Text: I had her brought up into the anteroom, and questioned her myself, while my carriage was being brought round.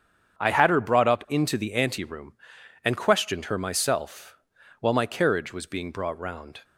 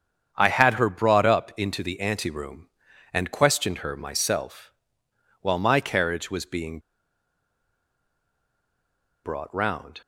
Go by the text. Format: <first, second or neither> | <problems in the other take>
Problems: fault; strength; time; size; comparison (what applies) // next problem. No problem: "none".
first | starts louder than the rest; strong; until 1.3 s; 7.5 dB; strong in the first // pauses between "being" and "brought"; strong; at 6.7 s; 2.4 s long